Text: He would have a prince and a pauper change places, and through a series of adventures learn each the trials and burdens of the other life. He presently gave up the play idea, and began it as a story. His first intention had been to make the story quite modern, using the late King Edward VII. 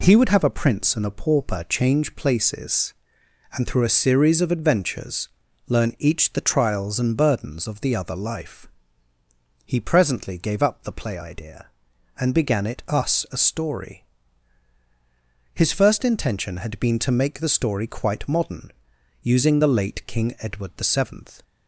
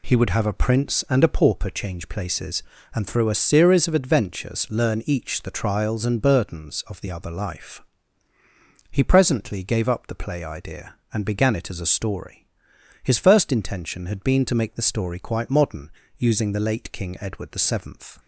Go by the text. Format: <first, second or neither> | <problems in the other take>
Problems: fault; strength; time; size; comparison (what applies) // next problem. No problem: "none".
second | pauses between "adventures" and "learn"; at 5.2 s; 0.40 s long // says "us" for "as"; at 12.8 s